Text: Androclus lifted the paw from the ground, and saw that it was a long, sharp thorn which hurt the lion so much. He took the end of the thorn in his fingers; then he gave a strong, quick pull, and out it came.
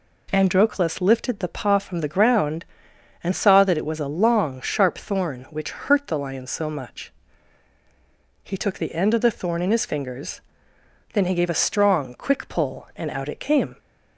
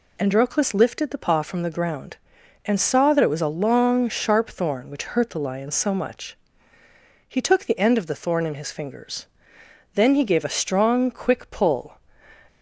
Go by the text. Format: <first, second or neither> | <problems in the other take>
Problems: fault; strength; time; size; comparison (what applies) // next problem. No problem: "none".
first | stops before "and out it came"; at 12.4 s